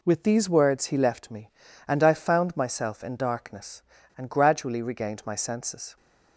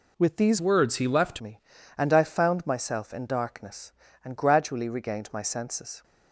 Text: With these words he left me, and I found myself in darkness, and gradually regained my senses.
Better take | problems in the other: first | changes voice from "words" to "left"; from 0.6 to 1.4 s; 0.8 s long

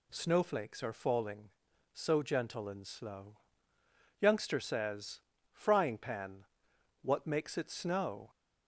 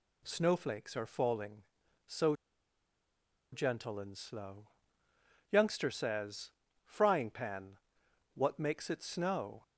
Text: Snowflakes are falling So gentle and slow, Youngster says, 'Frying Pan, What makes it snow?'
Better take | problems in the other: first | pauses between "So" and "gentle"; at 2.3 s; 1.1 s long

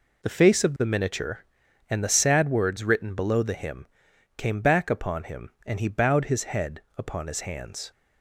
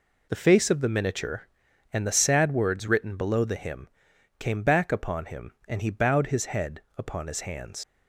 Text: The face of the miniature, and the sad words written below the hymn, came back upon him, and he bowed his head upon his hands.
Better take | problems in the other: first | pauses between "head" and "upon"; slight; at 6.8 s; 0.16 s long; slight in the first // leaves "hands" unfinished; at 7.8 s; 70 ms

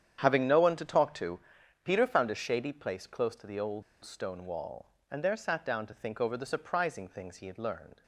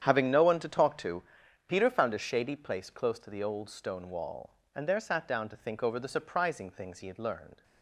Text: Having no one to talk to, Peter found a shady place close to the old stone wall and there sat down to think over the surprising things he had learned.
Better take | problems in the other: second | starts louder than the rest; strong; until 1.2 s; 9 dB; strong in the second // pauses between "old" and "stone"; slight; at 3.8 s; 0.21 s long

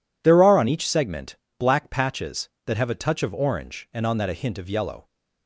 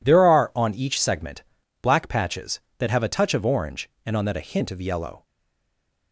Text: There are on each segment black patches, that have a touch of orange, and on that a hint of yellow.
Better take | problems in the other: first | pauses between "segment" and "black"; slight; at 1.4 s; 0.36 s long; slight in the first // stays silent after the last word; slight; from 5.2 s on; 0.9 s long

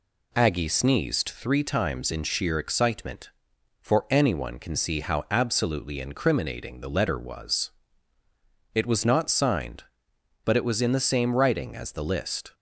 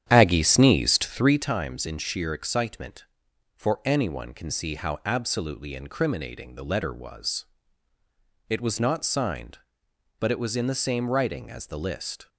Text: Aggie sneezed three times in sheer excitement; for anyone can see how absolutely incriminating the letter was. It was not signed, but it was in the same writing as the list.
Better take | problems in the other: first | starts louder than the rest; strong; until 1.6 s; 9.5 dB

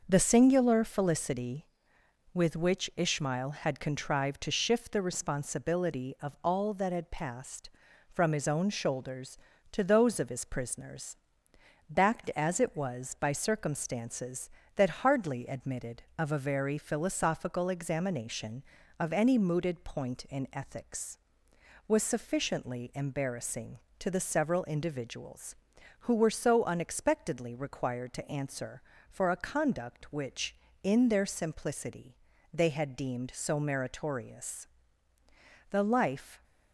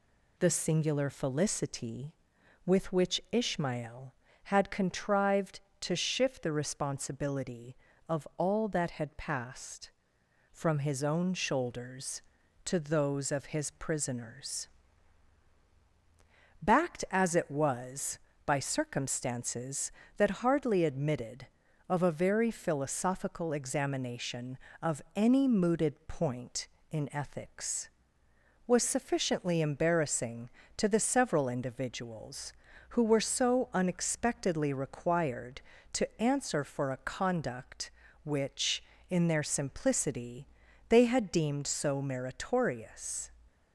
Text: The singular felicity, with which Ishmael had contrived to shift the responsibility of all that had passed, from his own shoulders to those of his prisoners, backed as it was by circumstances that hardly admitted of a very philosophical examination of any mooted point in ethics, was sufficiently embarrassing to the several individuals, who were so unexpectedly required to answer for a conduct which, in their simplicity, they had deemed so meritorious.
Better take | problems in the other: second | starts louder than the rest; noticeable; until 1.0 s; 6 dB // goes on to say "The life"; noticeable; from 35.7 s on; 0.72 s long

